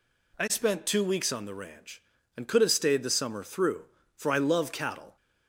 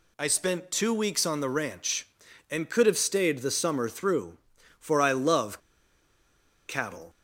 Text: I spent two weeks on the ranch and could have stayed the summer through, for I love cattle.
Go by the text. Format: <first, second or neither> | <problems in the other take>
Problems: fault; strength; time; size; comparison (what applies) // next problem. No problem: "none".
first | pauses between "love" and "cattle"; at 5.5 s; 1.1 s long